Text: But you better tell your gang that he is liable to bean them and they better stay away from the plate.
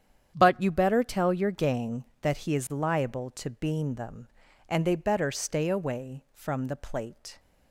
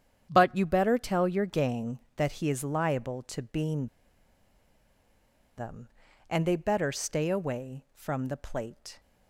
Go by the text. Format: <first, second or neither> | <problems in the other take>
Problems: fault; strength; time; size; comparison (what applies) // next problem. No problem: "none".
first | starts louder than the rest; strong; until 1.3 s; 9 dB; strong in the first // pauses between "bean" and "them"; strong; at 3.8 s; 1.6 s long